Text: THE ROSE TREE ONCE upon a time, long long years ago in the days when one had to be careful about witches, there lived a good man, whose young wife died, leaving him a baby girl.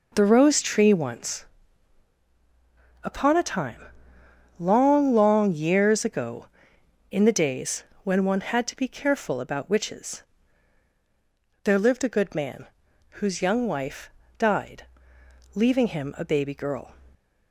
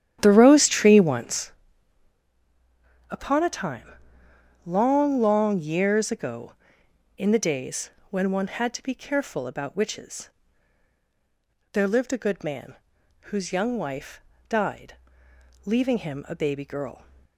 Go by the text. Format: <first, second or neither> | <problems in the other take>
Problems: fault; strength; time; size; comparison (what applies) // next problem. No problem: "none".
first | starts louder than the rest; strong; until 1.5 s; 11 dB // pauses between "ONCE" and "upon"; strong; at 1.5 s; 1.5 s long; strong in the first // pauses between "days" and "when"; slight; at 7.8 s; 0.20 s long; slight in the first // pauses between "wife" and "died"; slight; at 14.1 s; 0.28 s long; slight in the first